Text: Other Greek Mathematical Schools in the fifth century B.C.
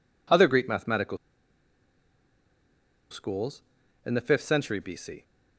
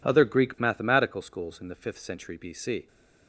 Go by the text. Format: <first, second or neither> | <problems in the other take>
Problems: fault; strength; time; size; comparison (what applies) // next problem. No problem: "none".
second | pauses between "Mathematical" and "Schools"; strong; at 1.1 s; 1.9 s long